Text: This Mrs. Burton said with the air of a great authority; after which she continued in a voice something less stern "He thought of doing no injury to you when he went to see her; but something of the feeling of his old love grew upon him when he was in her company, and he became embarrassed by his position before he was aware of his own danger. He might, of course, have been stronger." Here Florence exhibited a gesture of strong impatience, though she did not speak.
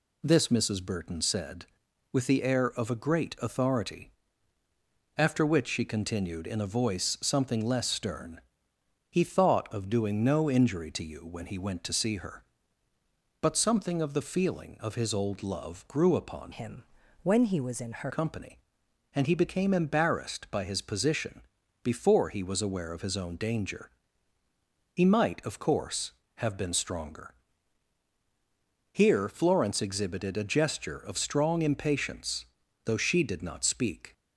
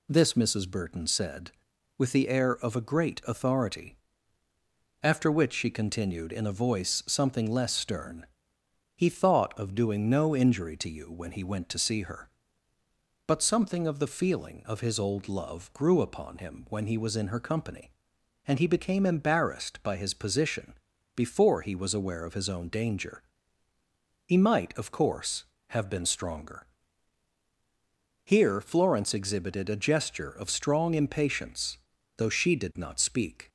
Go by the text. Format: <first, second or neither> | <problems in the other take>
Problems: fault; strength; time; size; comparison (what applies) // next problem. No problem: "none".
second | pauses between "stern" and "He"; noticeable; at 8.3 s; 0.70 s long; noticeable in the second // changes voice from "him" to "her"; from 16.5 to 18.1 s; 1.6 s long // pauses between "him" and "when"; at 16.8 s; 0.40 s long // pauses between "position" and "before"; at 21.4 s; 0.42 s long; also in the second